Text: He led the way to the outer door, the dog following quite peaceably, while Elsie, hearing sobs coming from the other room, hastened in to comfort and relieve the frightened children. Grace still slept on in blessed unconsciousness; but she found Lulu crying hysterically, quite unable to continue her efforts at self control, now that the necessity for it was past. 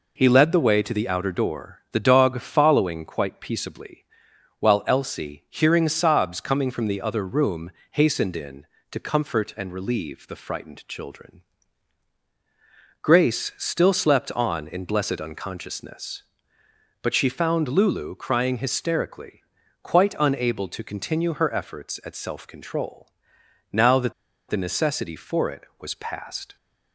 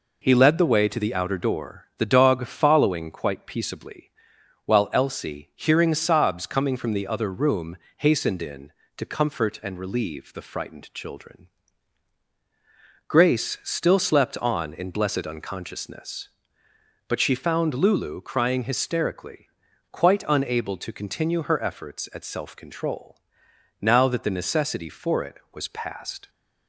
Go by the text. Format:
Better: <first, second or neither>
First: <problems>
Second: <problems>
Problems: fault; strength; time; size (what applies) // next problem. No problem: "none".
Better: second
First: pauses between "that" and "the"; at 24.1 s; 0.37 s long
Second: none